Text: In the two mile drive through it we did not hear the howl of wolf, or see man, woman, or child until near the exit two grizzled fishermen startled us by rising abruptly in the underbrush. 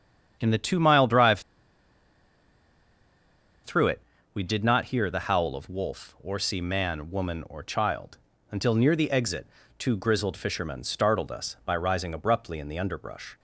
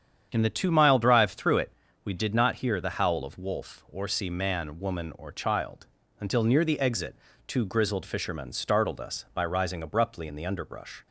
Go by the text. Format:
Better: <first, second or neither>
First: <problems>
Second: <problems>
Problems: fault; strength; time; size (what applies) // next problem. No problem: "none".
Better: second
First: starts louder than the rest; strong; until 1.4 s; 8.5 dB // pauses between "drive" and "through"; strong; at 1.3 s; 2.2 s long // pauses between "it" and "we"; slight; at 4.0 s; 0.32 s long // pauses between "child" and "until"; slight; at 8.1 s; 0.34 s long // pauses between "exit" and "two"; slight; at 9.4 s; 0.30 s long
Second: starts louder than the rest; strong; until 1.3 s; 8.5 dB // pauses between "it" and "we"; slight; at 1.7 s; 0.32 s long // pauses between "child" and "until"; slight; at 5.8 s; 0.34 s long // pauses between "exit" and "two"; slight; at 7.1 s; 0.30 s long